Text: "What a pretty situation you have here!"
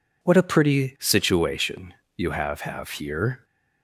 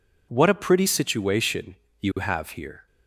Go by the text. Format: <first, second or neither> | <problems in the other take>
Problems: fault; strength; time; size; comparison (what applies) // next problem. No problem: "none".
second | pauses between "situation" and "you"; slight; at 1.9 s; 0.24 s long; slight in the second // says "have" twice; at 2.6 s